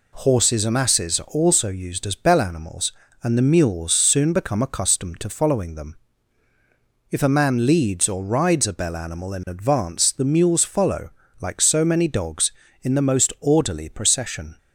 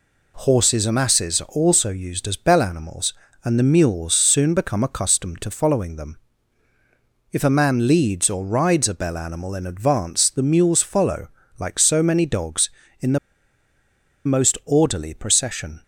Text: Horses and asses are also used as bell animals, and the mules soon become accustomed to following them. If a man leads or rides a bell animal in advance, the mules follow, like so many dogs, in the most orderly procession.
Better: first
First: none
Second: pauses between "the" and "most"; at 13.1 s; 1.0 s long

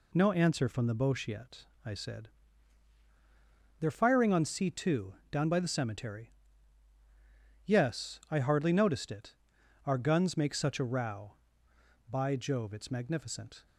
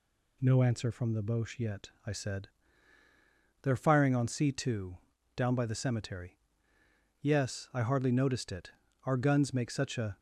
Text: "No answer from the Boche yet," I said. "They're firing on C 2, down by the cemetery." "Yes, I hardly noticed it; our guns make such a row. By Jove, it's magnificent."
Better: first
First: none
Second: stops before "row By Jove it's magnificent"; at 10.1 s

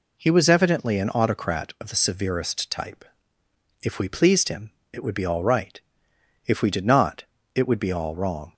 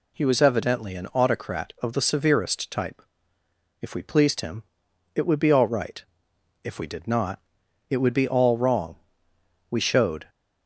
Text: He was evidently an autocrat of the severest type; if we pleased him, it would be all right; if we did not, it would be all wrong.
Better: first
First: none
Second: goes on to say "We showed"; from 9.7 s on; 0.58 s long

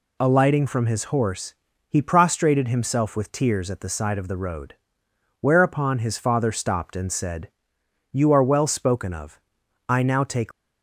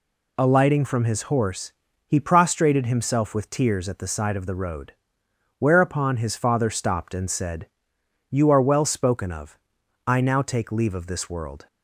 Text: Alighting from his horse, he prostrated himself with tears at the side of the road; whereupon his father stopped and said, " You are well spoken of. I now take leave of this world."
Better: second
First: stops before "leave of this world"; at 10.5 s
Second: none

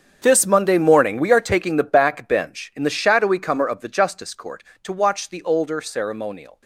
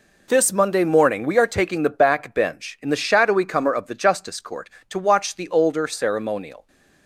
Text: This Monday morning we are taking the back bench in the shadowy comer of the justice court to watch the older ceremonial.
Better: second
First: gets quieter; strong; throughout; 15 dB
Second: none

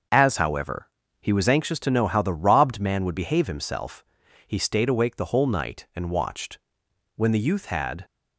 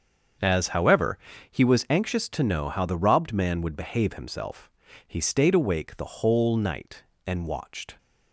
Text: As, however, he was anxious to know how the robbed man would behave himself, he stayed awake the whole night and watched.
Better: second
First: starts louder than the rest; until 1.4 s; 6.5 dB // goes on to say "When the youth had"; noticeable; from 7.1 s on; 0.88 s long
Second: starts louder than the rest; until 1.7 s; 7 dB

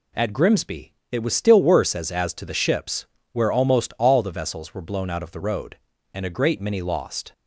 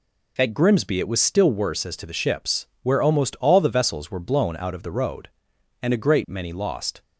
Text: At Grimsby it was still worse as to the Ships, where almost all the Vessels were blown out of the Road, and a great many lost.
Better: second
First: pauses between "Grimsby" and "it"; slight; at 0.9 s; 0.18 s long // says "as" twice; at 2.1 s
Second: none

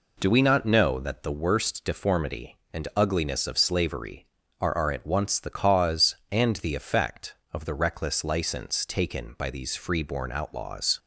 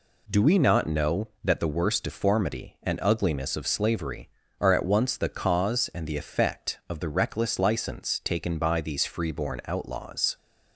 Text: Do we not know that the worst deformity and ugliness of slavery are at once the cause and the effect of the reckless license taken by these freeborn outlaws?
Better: second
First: says "are" twice; at 4.7 s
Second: none

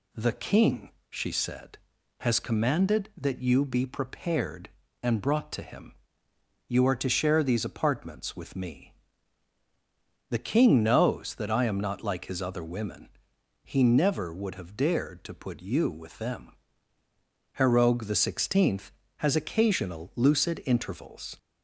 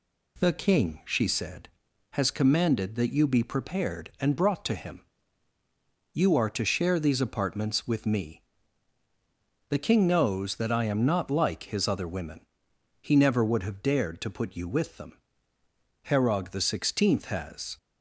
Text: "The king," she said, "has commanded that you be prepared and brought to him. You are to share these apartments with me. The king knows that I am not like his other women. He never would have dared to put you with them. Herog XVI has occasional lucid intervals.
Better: first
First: none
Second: stops before "occasional lucid intervals"; at 17.7 s

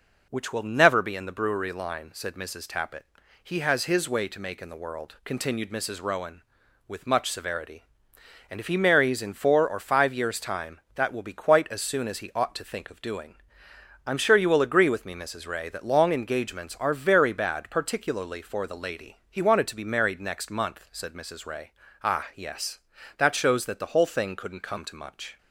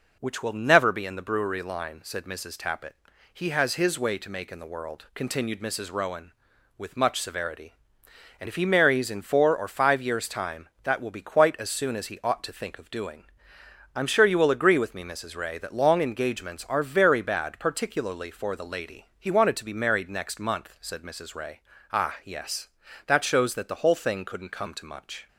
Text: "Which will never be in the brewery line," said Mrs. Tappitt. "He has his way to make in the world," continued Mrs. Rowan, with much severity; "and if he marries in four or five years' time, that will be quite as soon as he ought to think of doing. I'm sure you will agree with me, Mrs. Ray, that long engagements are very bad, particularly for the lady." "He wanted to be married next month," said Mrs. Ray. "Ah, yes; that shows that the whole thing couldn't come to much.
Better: neither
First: none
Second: none

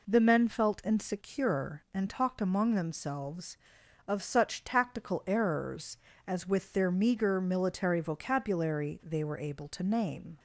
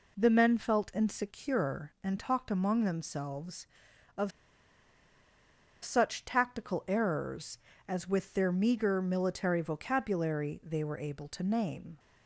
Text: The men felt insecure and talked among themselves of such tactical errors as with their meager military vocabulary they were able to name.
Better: first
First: none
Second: pauses between "of" and "such"; strong; at 4.3 s; 1.5 s long

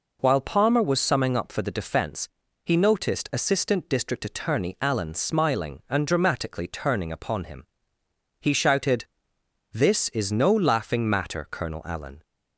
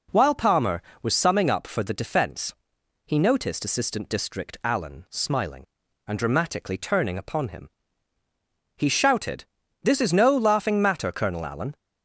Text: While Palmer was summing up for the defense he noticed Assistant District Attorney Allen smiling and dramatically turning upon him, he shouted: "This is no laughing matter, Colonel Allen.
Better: first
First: pauses between "defense" and "he"; slight; at 2.2 s; 0.34 s long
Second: pauses between "defense" and "he"; noticeable; at 2.5 s; 0.52 s long // skips "Attorney"; at 4.6 s

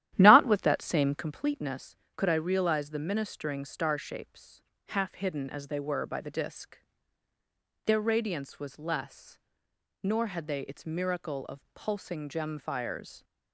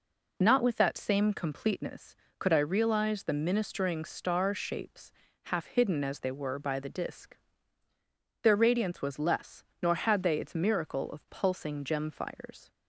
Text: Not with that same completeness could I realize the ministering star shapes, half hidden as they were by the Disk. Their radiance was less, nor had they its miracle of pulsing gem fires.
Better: second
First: starts louder than the rest; strong; until 1.3 s; 12.5 dB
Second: none

